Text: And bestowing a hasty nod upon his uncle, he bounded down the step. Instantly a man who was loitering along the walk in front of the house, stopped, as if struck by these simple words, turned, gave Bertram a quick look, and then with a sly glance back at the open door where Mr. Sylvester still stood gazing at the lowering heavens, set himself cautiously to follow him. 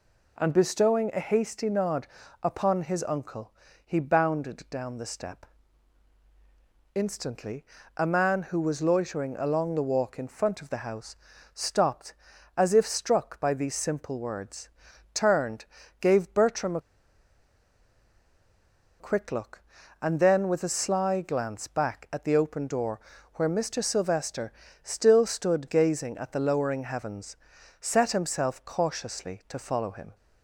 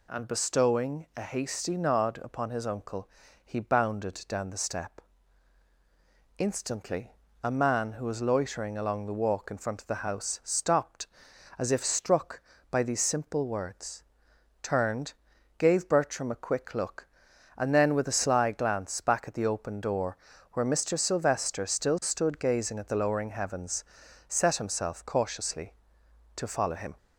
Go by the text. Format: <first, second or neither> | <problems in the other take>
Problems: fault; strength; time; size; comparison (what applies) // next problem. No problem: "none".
second | pauses between "nod" and "upon"; at 2.0 s; 0.38 s long // pauses between "Instantly" and "a"; slight; at 7.6 s; 0.32 s long; slight in the second // pauses between "a" and "quick"; strong; at 16.8 s; 2.1 s long // pauses between "door" and "where"; slight; at 23.0 s; 0.34 s long; slight in the second // pauses between "Sylvester" and "still"; slight; at 24.5 s; 0.30 s long